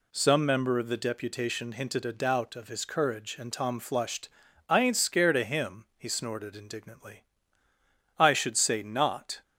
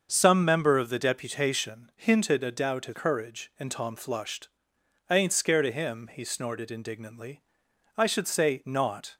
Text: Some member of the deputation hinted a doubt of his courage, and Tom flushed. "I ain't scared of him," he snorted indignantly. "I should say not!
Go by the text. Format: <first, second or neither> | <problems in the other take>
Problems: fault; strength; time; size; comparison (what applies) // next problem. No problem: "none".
first | starts louder than the rest; until 1.1 s; 6.5 dB // skips "his"; at 2.9 s